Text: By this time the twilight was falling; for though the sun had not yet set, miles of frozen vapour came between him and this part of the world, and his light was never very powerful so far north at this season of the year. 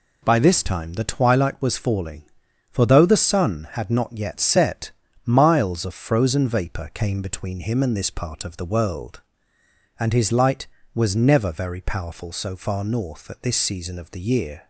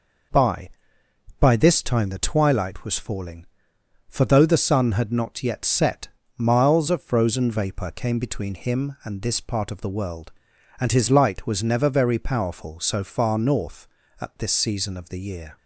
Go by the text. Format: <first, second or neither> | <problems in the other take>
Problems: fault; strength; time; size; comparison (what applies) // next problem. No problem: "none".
first | says "By" twice; at 1.3 s